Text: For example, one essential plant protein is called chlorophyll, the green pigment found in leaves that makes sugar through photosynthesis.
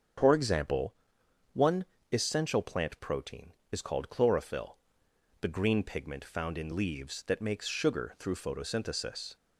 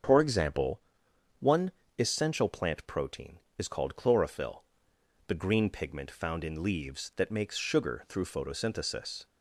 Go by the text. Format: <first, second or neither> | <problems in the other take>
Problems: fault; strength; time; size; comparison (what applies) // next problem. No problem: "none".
neither | starts louder than the rest; the same in both // pauses between "one" and "essential"; slight; the same in both